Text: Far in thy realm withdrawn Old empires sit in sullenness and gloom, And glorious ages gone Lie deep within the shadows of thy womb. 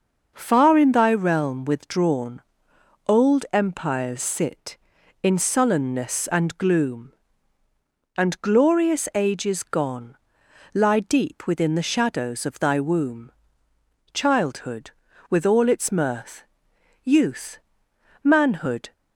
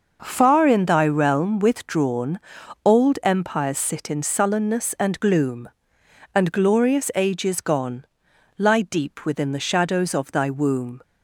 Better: second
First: starts louder than the rest; until 1.3 s; 6 dB // pauses between "withdrawn" and "Old"; noticeable; at 2.4 s; 0.64 s long // pauses between "gone" and "Lie"; noticeable; at 10.1 s; 0.58 s long // goes on to say "Childhood with all its mirth Youth Manhood"; strong; from 14.1 s on; 4.7 s long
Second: pauses between "withdrawn" and "Old"; noticeable; at 2.3 s; 0.46 s long // pauses between "gone" and "Lie"; noticeable; at 8.0 s; 0.52 s long

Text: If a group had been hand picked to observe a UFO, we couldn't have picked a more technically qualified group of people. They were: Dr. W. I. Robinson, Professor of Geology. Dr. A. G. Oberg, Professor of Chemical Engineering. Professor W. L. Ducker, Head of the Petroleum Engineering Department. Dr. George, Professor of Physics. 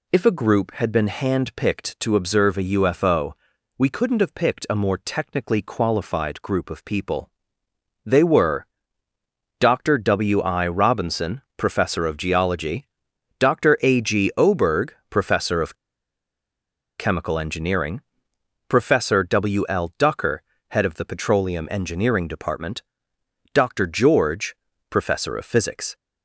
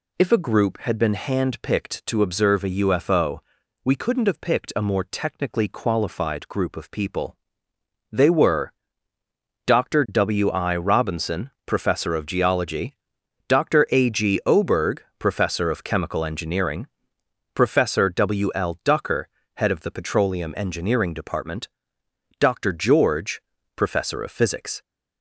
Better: second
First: pauses between "of" and "Chemical"; strong; at 15.7 s; 1.2 s long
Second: none

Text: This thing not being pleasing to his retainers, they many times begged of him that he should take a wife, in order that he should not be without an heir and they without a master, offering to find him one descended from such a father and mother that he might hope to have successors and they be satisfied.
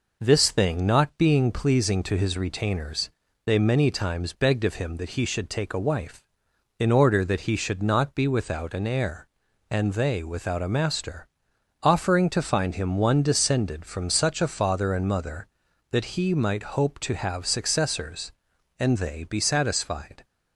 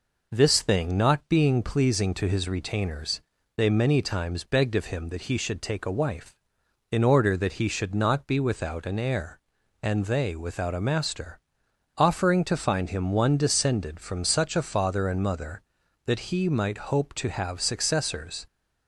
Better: first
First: none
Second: stops before "and they be satisfied"; at 18.4 s

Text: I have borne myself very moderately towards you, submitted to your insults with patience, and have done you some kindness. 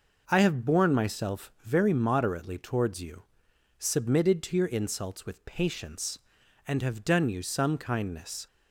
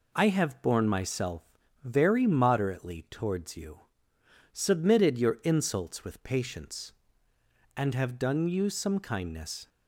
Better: first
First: none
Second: pauses between "myself" and "very"; at 1.4 s; 0.40 s long // skips "to"; at 5.1 s

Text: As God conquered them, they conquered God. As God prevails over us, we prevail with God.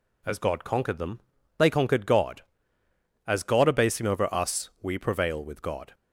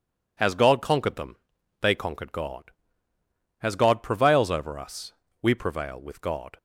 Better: second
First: says "abasing" for "prevails"; at 3.6 s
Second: none

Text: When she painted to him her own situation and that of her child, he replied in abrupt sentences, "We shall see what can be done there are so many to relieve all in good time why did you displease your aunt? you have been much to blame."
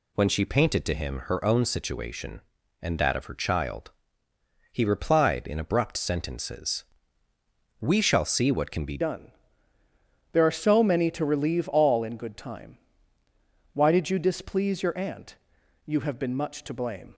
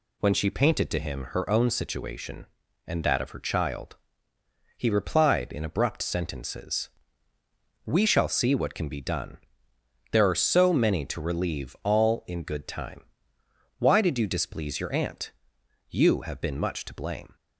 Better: second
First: changes voice at "done"; from 9.0 s on; 8.1 s long // pauses between "done" and "there"; at 9.3 s; 1.0 s long // pauses between "time" and "why"; noticeable; at 12.7 s; 0.98 s long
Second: pauses between "done" and "there"; noticeable; at 9.3 s; 0.74 s long // pauses between "time" and "why"; noticeable; at 13.0 s; 0.76 s long

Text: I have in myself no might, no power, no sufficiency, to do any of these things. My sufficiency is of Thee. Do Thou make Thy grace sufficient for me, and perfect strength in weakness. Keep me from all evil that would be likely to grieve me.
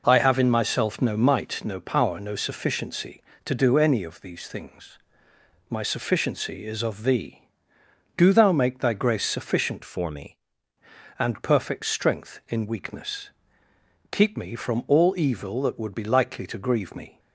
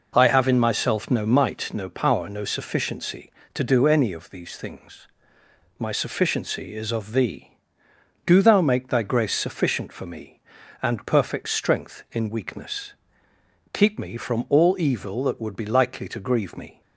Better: second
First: changes voice from "for" to "me"; from 9.8 to 10.3 s; 0.5 s long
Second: none

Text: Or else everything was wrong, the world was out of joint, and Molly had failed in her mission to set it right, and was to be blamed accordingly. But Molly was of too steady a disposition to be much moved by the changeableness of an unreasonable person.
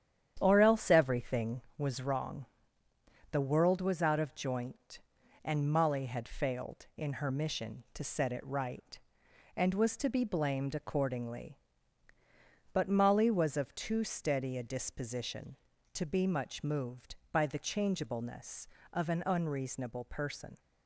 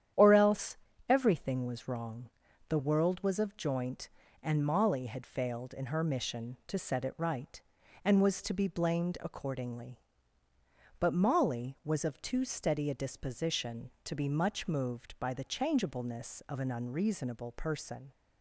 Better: first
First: starts louder than the rest; strong; until 1.4 s; 9.5 dB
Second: starts louder than the rest; strong; until 1.4 s; 10 dB // pauses between "else" and "everything"; slight; at 0.7 s; 0.32 s long // skips "out"; at 3.3 s

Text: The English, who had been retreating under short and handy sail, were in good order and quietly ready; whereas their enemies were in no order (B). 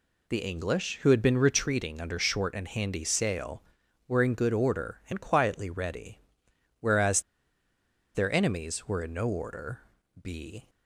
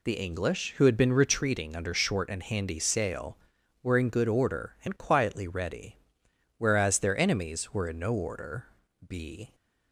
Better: second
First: pauses between "whereas" and "their"; noticeable; at 7.2 s; 0.93 s long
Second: none

